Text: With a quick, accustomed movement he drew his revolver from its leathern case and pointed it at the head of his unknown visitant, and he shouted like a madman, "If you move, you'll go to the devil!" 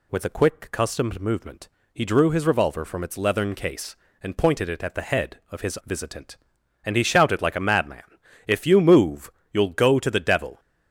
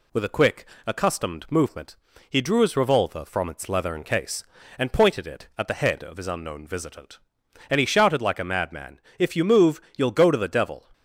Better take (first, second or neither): second